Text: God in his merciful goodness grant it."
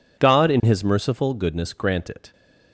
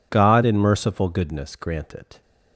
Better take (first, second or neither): first